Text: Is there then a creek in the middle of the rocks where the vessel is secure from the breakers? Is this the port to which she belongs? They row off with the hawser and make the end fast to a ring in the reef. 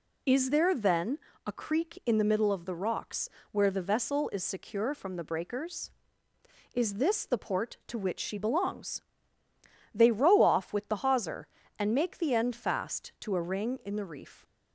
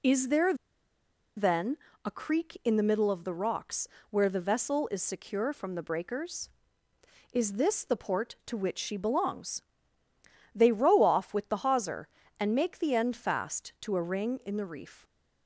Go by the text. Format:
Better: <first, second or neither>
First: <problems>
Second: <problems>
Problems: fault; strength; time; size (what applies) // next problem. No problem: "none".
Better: first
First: pauses between "then" and "a"; slight; at 1.1 s; 0.30 s long // pauses between "rocks" and "where"; slight; at 3.2 s; 0.24 s long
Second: pauses between "there" and "then"; noticeable; at 0.5 s; 0.82 s long // pauses between "then" and "a"; slight; at 1.7 s; 0.30 s long // pauses between "rocks" and "where"; slight; at 3.8 s; 0.24 s long